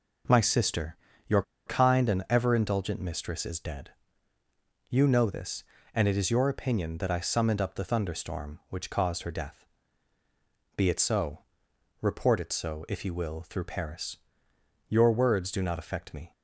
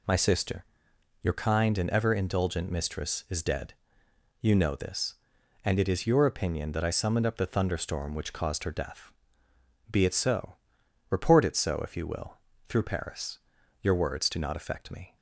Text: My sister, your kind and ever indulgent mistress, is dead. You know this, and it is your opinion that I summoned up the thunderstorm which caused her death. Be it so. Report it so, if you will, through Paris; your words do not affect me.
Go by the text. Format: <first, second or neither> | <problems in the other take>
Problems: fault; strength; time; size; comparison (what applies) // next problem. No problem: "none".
second | pauses between "your" and "kind"; slight; at 1.4 s; 0.24 s long